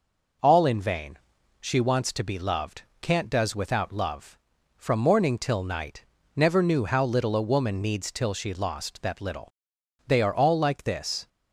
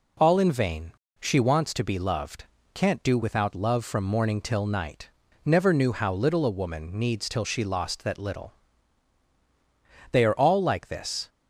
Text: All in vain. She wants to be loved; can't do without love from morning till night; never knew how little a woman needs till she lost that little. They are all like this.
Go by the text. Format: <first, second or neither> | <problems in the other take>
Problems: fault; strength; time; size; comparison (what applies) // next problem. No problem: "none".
second | says "does" for "do"; at 3.2 s